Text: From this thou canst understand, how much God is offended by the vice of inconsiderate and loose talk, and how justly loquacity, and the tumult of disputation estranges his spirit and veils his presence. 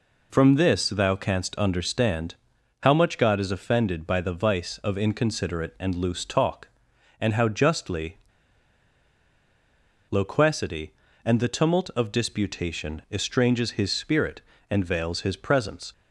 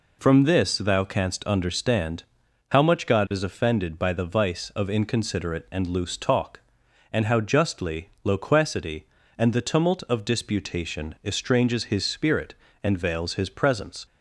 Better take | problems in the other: second | pauses between "justly" and "loquacity"; strong; at 8.1 s; 1.9 s long

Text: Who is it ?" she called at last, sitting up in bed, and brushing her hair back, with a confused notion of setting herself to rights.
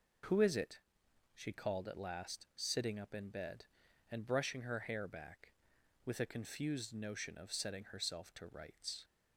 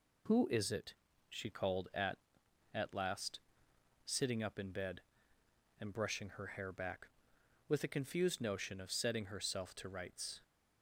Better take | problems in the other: first | says "at" twice; at 2.7 s

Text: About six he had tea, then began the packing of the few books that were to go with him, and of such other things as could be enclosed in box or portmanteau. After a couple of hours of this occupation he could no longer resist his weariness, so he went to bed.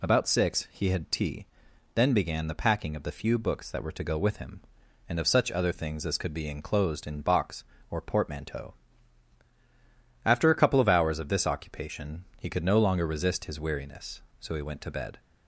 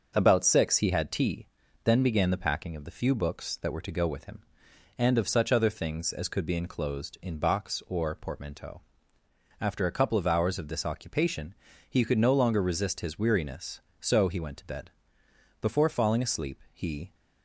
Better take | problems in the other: first | starts louder than the rest; until 1.1 s; 6.5 dB // pauses between "occupation" and "he"; slight; at 11.5 s; 0.36 s long // goes on to say "Before falling asleep he"; from 15.6 s on; 1.5 s long

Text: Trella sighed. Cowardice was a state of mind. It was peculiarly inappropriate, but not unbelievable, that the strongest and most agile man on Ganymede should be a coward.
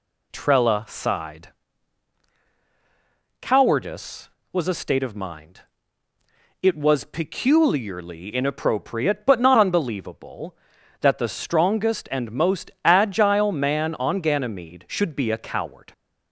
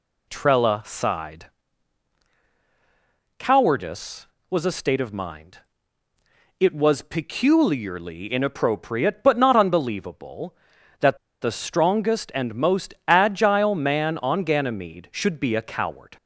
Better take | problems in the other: first | pauses between "that" and "the"; slight; at 11.1 s; 0.24 s long

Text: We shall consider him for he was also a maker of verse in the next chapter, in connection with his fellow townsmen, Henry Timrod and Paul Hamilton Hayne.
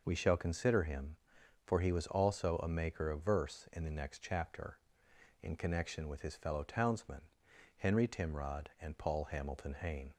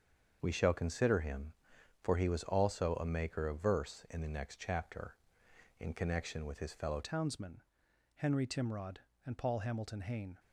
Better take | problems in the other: first | starts louder than the rest; until 1.4 s; 7 dB // changes voice at "townsmen"; from 7.0 s on; 3.3 s long

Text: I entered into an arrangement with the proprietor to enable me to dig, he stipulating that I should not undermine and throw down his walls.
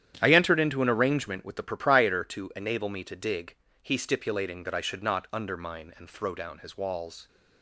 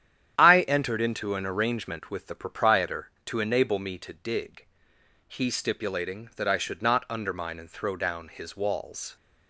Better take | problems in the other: neither | starts louder than the rest; strong; the same in both

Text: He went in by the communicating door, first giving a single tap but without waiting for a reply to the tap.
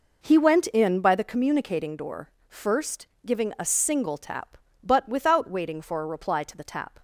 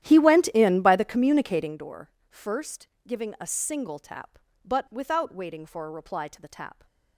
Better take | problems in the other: first | starts louder than the rest; strong; until 1.9 s; 12 dB // pauses between "first" and "giving"; slight; at 2.8 s; 0.20 s long; slight in the first

